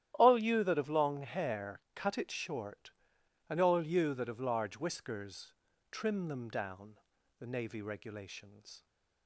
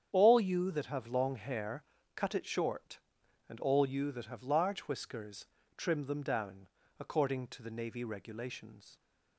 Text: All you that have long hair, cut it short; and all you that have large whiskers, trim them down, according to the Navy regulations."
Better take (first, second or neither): second